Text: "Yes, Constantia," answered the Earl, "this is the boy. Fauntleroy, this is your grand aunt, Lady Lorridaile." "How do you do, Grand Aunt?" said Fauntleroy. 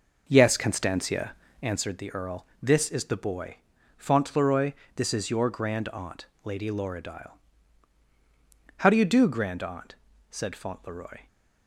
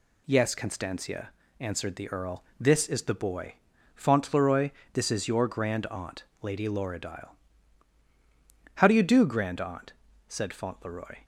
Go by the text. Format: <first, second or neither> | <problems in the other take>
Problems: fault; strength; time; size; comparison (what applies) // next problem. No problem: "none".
second | starts louder than the rest; noticeable; until 1.9 s; 5.5 dB